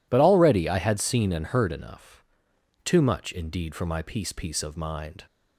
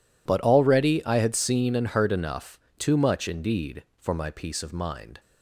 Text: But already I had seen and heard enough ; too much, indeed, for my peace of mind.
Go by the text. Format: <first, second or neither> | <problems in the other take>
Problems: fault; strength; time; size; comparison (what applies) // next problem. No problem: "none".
second | says "peace" twice; at 4.3 s